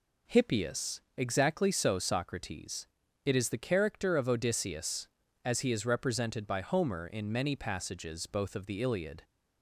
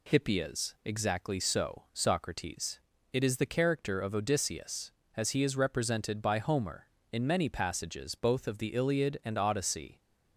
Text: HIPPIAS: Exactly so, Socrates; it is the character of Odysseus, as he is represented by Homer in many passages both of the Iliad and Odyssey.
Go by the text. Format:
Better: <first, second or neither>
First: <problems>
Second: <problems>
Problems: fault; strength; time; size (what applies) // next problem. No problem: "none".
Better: second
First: stops before "and Odyssey"; at 9.2 s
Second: none